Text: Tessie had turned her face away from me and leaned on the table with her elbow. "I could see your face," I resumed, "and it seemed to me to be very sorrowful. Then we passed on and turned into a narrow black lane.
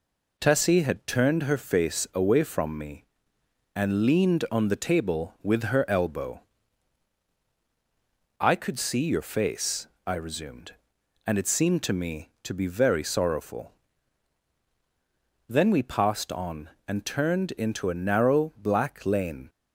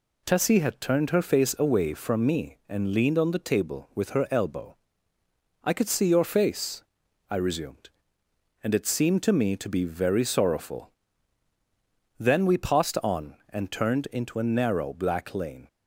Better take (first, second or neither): neither